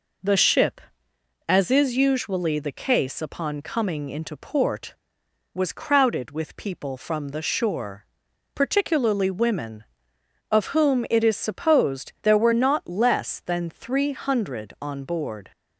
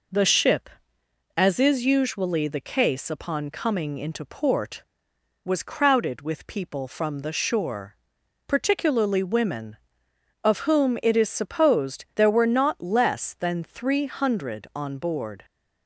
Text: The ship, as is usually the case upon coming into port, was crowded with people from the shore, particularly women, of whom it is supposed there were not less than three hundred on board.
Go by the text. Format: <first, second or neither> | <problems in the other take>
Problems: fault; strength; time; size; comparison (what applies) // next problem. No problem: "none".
neither | none